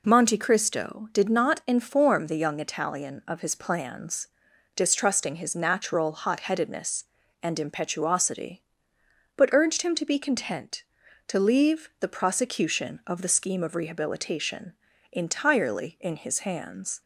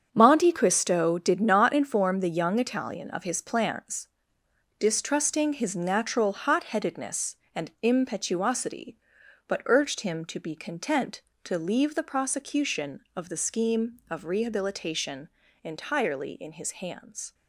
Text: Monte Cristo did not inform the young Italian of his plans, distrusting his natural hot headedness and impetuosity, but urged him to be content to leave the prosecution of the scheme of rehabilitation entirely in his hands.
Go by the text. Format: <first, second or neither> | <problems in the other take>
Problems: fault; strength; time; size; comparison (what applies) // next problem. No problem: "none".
first | gets quieter; strong; throughout; 10.5 dB // pauses between "rehabilitation" and "entirely"; slight; at 15.2 s; 0.34 s long; also in the first